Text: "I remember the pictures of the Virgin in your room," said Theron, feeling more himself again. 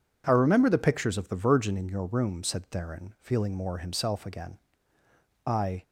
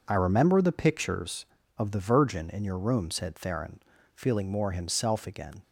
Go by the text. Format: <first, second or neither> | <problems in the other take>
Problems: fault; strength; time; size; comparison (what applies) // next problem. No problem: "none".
second | goes on to say "I"; slight; from 5.4 s on; 0.38 s long